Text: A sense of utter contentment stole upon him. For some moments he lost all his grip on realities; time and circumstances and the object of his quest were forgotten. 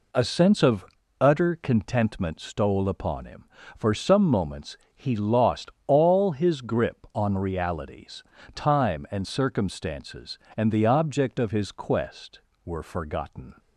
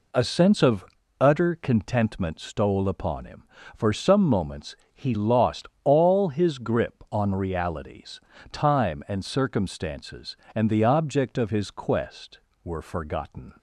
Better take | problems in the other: neither | pauses between "of" and "utter"; slight; the same in both // pauses between "moments" and "he"; slight; the same in both // pauses between "lost" and "all"; slight; the same in both

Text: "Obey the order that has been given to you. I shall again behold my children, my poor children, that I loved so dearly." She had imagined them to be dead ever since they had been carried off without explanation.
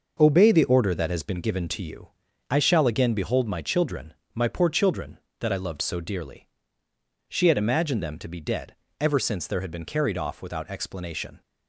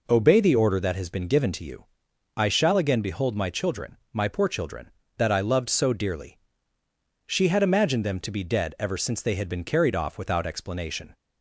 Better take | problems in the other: second | pauses between "dead" and "ever"; slight; at 8.7 s; 0.24 s long // says "there" for "they"; at 9.4 s

